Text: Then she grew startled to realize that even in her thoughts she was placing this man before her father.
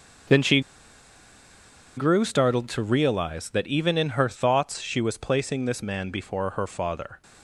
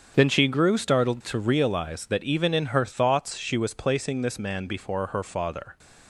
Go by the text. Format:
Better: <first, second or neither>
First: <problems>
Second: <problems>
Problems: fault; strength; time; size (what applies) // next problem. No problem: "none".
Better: second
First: starts louder than the rest; strong; until 2.6 s; 8 dB // pauses between "she" and "grew"; strong; at 0.6 s; 1.3 s long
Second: starts louder than the rest; strong; until 1.1 s; 8 dB